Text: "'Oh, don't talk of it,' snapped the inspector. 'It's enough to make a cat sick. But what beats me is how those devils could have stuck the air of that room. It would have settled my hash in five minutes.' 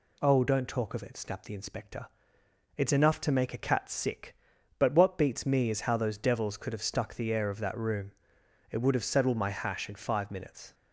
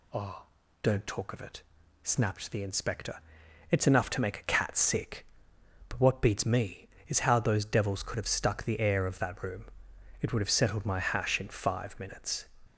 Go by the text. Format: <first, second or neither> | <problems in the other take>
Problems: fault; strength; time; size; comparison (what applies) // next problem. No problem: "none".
neither | none